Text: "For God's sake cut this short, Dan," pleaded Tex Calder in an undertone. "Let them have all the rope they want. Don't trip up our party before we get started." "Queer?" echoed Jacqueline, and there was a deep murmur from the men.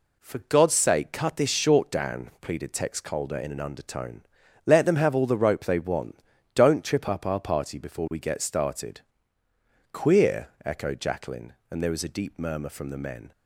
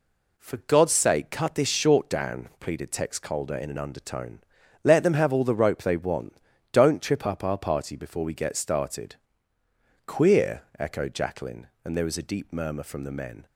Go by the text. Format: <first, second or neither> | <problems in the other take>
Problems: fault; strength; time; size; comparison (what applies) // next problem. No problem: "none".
neither | none